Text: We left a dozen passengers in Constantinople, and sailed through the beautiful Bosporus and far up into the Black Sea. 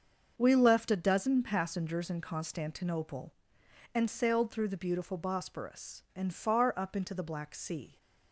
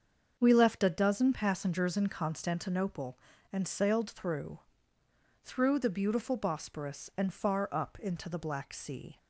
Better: first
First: starts louder than the rest; until 1.3 s; 6.5 dB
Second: starts louder than the rest; until 1.4 s; 6.5 dB // says "through" twice; at 5.4 s

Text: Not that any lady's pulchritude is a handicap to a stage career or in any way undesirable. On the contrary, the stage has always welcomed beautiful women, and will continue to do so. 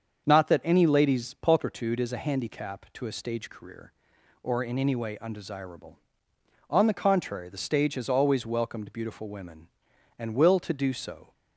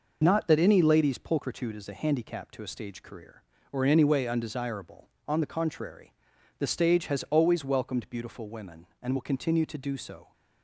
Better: second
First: starts louder than the rest; until 1.2 s; 7 dB // skips "continue"; at 10.5 s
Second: none

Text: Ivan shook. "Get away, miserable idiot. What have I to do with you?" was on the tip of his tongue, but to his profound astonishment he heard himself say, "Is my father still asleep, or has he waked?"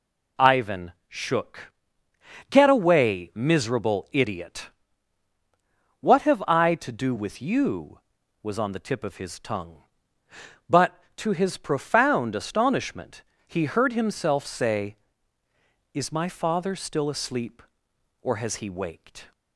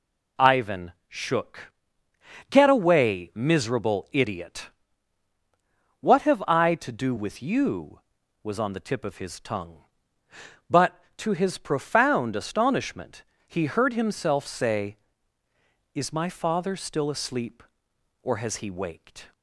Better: neither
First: pauses between "Ivan" and "shook"; slight; at 0.9 s; 0.16 s long // pauses between "astonishment" and "he"; slight; at 13.2 s; 0.22 s long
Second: pauses between "Ivan" and "shook"; slight; at 0.9 s; 0.16 s long // pauses between "astonishment" and "he"; slight; at 13.2 s; 0.22 s long

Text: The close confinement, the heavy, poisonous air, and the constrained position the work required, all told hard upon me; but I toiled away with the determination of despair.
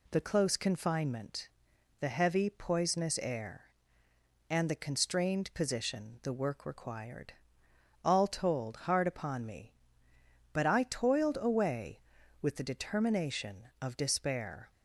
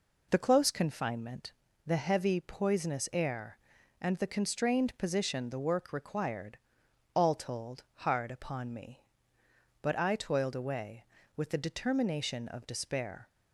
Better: neither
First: none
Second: none

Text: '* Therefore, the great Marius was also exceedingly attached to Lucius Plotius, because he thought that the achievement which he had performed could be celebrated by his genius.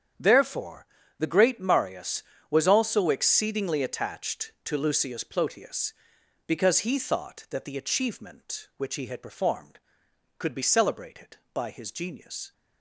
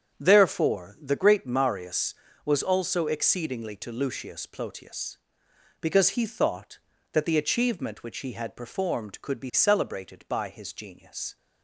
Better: first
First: starts louder than the rest; strong; until 1.4 s; 8 dB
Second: starts louder than the rest; strong; until 1.2 s; 7.5 dB // skips "attached"; at 3.7 s

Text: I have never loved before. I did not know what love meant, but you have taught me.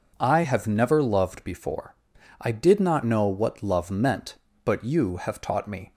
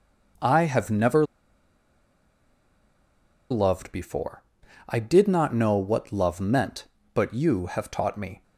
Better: first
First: none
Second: pauses between "never" and "loved"; strong; at 1.2 s; 2.2 s long

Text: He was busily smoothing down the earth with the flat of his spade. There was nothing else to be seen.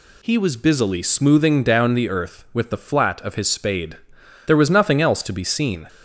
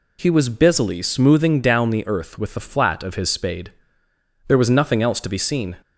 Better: neither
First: none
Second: none

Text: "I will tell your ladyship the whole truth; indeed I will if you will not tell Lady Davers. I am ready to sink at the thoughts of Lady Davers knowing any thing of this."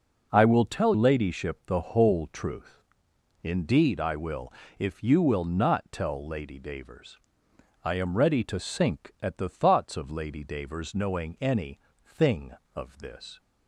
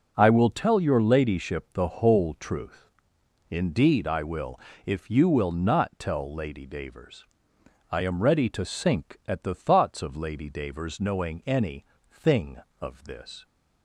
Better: second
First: skips "your"; at 0.9 s // pauses between "will" and "if"; slight; at 4.5 s; 0.24 s long // pauses between "any" and "thing"; slight; at 11.7 s; 0.24 s long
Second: pauses between "will" and "if"; slight; at 4.6 s; 0.24 s long // pauses between "any" and "thing"; slight; at 11.8 s; 0.24 s long

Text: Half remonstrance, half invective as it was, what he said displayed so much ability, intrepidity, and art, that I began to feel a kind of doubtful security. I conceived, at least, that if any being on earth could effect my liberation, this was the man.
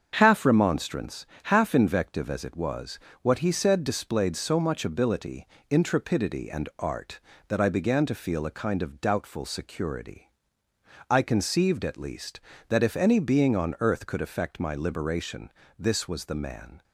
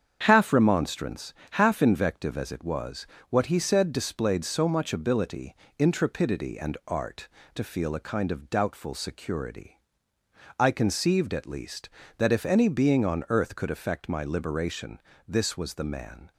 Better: first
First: starts louder than the rest; until 1.1 s; 7 dB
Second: starts louder than the rest; strong; until 1.2 s; 8 dB // skips "that I began"; at 7.4 s

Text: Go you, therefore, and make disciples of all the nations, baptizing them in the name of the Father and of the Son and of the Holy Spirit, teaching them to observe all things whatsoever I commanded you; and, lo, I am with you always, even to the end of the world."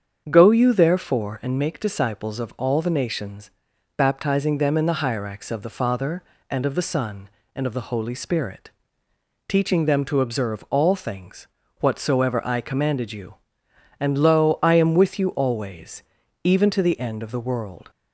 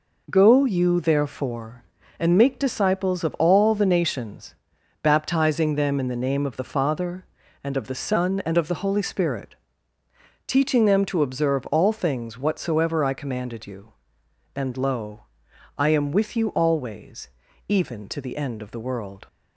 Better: second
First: starts louder than the rest; strong; until 1.3 s; 7.5 dB // says "hyrax" for "name"; at 4.9 s // pauses between "things" and "whatsoever"; slight; at 11.4 s; 0.34 s long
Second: none

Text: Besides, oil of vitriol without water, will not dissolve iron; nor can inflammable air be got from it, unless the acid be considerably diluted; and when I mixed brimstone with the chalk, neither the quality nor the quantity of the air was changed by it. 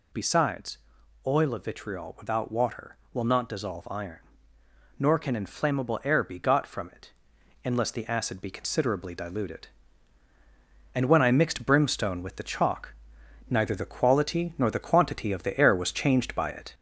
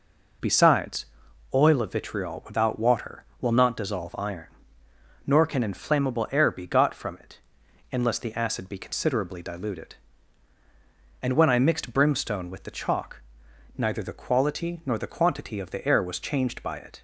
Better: second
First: gets louder; slight; throughout; 2.5 dB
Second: none

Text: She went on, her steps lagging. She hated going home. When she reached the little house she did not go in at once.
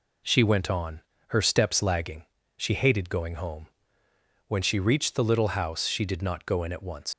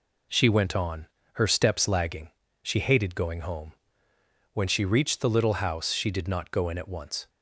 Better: second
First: leaves "once" unfinished; at 7.1 s; 105 ms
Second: none

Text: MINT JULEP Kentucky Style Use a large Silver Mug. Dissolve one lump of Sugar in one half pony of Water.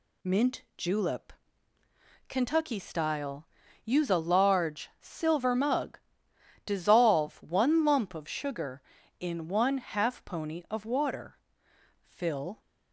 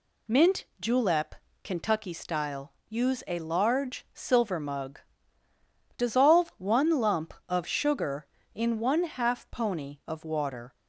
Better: second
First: pauses between "MINT" and "JULEP"; slight; at 0.6 s; 0.16 s long // pauses between "JULEP" and "Kentucky"; noticeable; at 1.3 s; 0.96 s long // pauses between "Style" and "Use"; at 3.4 s; 0.38 s long // goes on to say "Fill"; from 12.0 s on; 0.58 s long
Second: pauses between "JULEP" and "Kentucky"; slight; at 1.3 s; 0.30 s long // pauses between "Style" and "Use"; slight; at 2.7 s; 0.16 s long

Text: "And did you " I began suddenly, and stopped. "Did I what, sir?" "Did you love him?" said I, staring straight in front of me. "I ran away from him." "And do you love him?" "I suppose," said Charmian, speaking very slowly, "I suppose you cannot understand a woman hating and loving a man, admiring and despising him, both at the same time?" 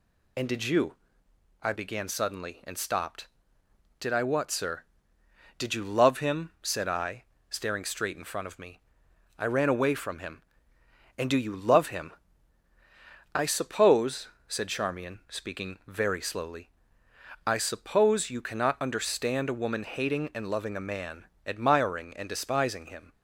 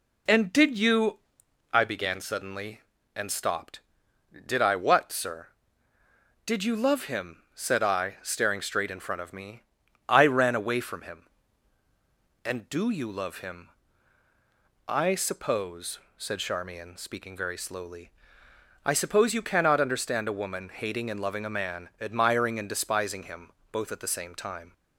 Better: second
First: stops before "both at the same time"; at 23.1 s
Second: none

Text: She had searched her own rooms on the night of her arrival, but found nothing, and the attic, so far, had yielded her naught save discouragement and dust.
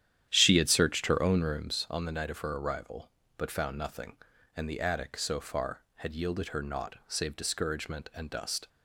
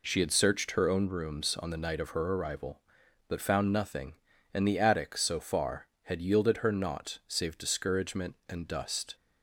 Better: second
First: starts louder than the rest; strong; until 1.8 s; 11 dB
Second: none

